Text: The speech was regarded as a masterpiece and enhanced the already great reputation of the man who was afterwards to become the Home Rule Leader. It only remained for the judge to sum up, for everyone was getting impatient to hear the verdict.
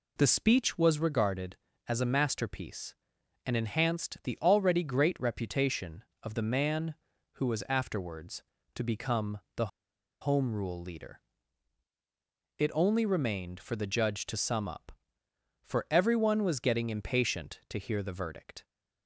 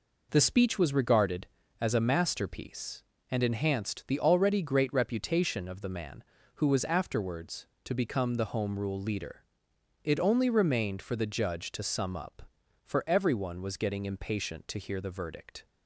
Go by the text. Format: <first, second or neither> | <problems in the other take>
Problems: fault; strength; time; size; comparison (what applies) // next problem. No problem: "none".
second | pauses between "become" and "the"; slight; at 9.3 s; 0.20 s long // pauses between "the" and "Home"; noticeable; at 9.6 s; 0.54 s long